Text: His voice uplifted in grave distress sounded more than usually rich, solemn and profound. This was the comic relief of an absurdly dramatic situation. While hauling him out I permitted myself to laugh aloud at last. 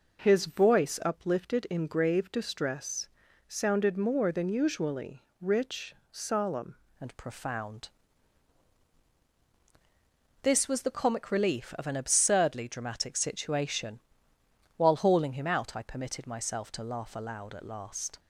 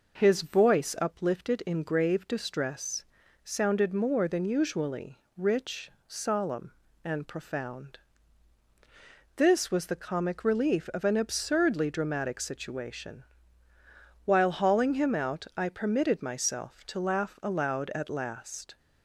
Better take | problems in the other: second | pauses between "distress" and "sounded"; at 3.0 s; 0.40 s long; also in the second // pauses between "usually" and "rich"; slight; at 5.2 s; 0.18 s long; slight in the second // changes voice at "and"; from 7.0 s on; 11.1 s long

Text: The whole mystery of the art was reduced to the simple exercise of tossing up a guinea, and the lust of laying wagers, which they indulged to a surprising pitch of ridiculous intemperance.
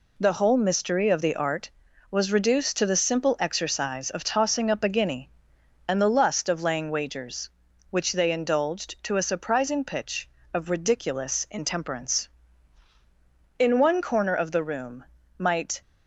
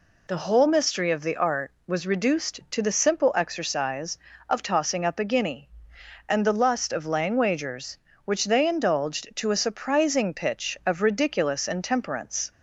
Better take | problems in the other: second | goes on to say "In one corner of the room might"; strong; from 13.5 s on; 2.2 s long

